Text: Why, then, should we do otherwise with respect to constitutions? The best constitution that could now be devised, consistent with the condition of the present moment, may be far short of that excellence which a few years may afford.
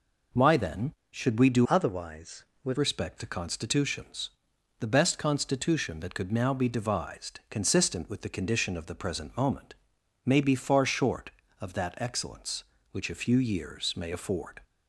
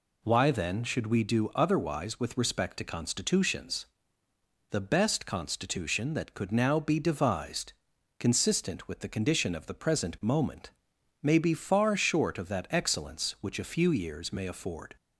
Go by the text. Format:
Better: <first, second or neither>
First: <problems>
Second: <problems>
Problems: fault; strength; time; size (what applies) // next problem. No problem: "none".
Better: second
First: changes voice from "otherwise" to "with"; from 1.6 to 2.7 s; 1.1 s long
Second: none